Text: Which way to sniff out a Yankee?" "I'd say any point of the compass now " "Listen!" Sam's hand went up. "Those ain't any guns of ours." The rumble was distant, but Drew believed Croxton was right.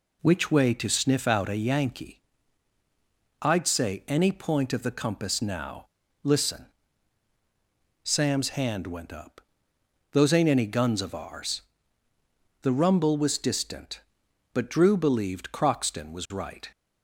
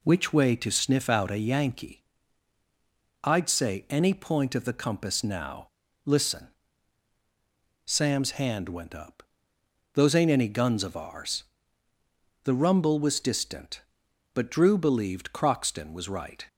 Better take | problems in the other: neither | none

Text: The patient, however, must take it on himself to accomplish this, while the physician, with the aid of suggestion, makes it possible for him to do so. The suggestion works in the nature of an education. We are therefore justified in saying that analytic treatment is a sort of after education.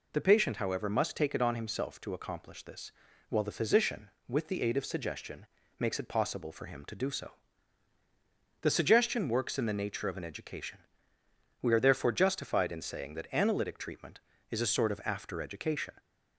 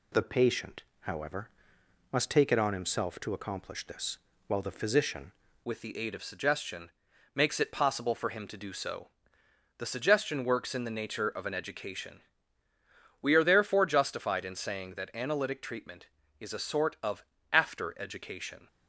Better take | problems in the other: first | changes voice at "with"; from 5.6 s on; 13.0 s long // pauses between "of" and "after"; slight; at 17.2 s; 0.26 s long

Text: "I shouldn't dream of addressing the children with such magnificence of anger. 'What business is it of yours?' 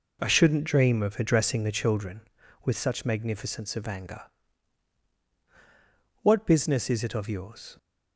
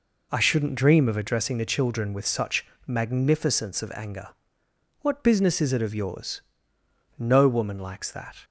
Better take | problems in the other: first | pauses between "such" and "magnificence"; slight; at 2.6 s; 0.22 s long // goes on to say "No woman likes that"; noticeable; from 7.1 s on; 1.1 s long

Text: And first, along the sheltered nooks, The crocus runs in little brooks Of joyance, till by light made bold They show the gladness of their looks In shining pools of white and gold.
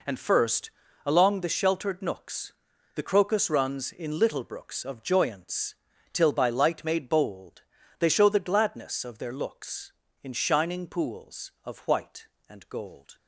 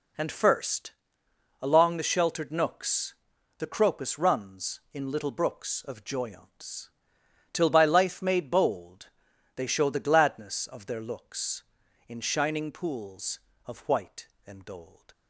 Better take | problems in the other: first | says "life" for "light"; at 7.8 s // pauses between "bold" and "They"; noticeable; at 9.0 s; 0.46 s long; also in the first

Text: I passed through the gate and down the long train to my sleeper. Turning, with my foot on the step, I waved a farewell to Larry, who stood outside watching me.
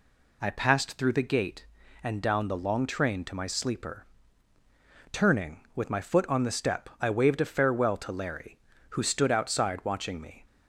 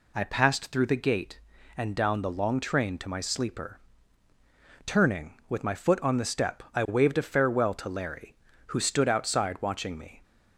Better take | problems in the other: neither | none

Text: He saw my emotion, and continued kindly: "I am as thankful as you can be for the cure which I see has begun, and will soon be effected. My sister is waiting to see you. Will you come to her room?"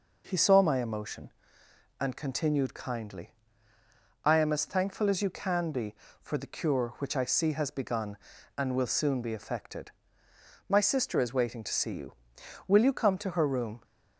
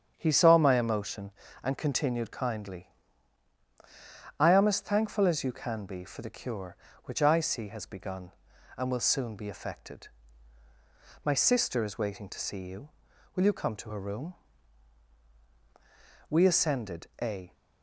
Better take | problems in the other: first | starts louder than the rest; strong; until 1.1 s; 8 dB // goes on to say "We ascended a"; noticeable; from 16.2 s on; 1.2 s long

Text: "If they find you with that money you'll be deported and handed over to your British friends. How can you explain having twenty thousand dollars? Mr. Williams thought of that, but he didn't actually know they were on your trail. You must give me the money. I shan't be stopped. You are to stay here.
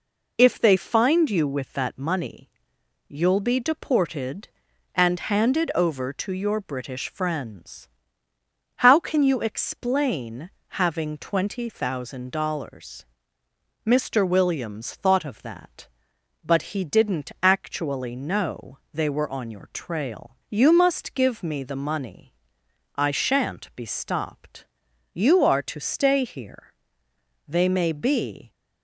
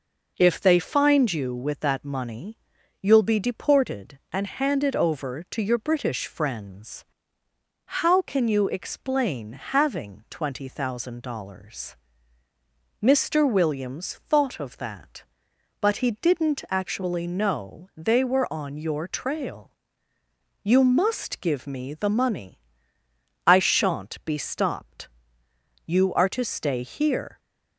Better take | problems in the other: second | pauses between "money" and "you'll"; noticeable; at 2.4 s; 0.58 s long; also in the second // pauses between "explain" and "having"; slight; at 10.4 s; 0.32 s long // goes on to say "They may be"; noticeable; from 27.4 s on; 1.0 s long

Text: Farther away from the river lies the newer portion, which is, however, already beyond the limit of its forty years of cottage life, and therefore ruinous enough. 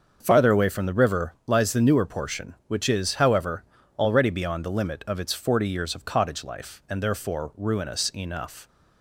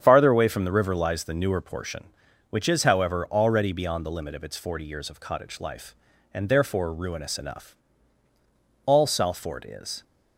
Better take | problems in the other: first | starts louder than the rest; strong; until 1.0 s; 8 dB; also in the first // goes on to say "All Salford is"; noticeable; from 8.8 s on; 1.1 s long

